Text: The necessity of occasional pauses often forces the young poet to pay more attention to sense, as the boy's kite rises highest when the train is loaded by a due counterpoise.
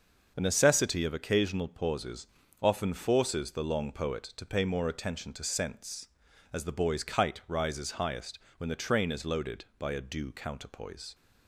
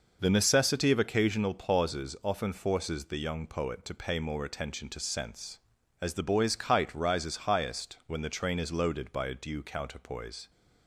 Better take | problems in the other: second | starts louder than the rest; noticeable; until 1.3 s; 6 dB // pauses between "pauses" and "often"; slight; at 2.2 s; 0.34 s long // says "long" for "young"; at 3.6 s // pauses between "highest" and "when"; slight; at 8.3 s; 0.18 s long

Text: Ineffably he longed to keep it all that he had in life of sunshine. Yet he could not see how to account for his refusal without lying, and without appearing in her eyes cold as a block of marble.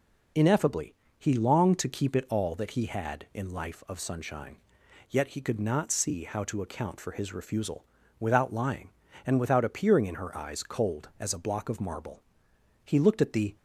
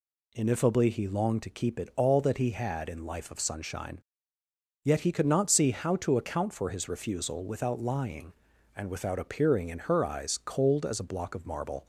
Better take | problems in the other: second | pauses between "Ineffably" and "he"; slight; at 0.9 s; 0.24 s long // pauses between "refusal" and "without"; slight; at 7.8 s; 0.36 s long // goes on to say "He looked at the"; noticeable; from 12.8 s on; 0.70 s long

